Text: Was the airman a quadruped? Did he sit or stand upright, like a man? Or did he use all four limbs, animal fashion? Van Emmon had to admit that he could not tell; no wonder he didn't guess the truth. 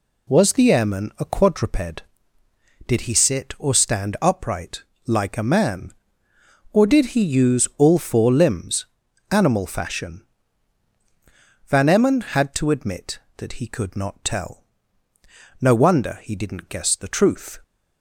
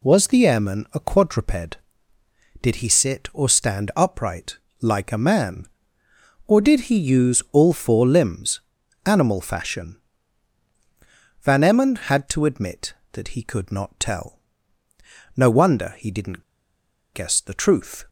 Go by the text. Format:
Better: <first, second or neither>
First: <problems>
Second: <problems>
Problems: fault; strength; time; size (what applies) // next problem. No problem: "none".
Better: first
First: none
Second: pauses between "didn't" and "guess"; noticeable; at 16.4 s; 0.70 s long